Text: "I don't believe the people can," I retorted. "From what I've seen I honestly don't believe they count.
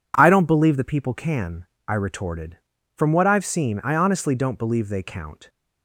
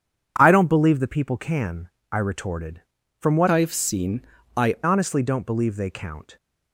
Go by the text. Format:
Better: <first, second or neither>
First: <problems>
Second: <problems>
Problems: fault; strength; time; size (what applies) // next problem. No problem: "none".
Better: first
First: none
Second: changes voice from "I've" to "I"; from 3.4 to 4.7 s; 1.3 s long // pauses between "seen" and "I"; slight; at 4.2 s; 0.34 s long